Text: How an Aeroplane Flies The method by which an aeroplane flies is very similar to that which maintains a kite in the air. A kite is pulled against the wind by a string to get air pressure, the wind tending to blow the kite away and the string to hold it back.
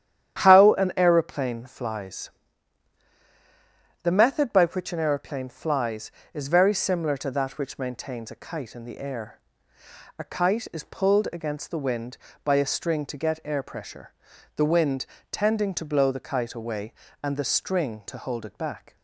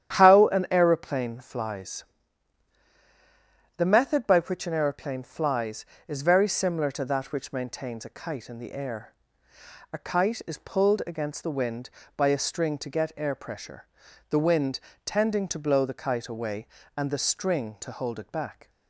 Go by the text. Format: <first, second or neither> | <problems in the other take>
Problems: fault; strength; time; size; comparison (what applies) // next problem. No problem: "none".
neither | starts louder than the rest; strong; the same in both // pauses between "Flies" and "The"; strong; the same in both // pauses between "wind" and "tending"; slight; the same in both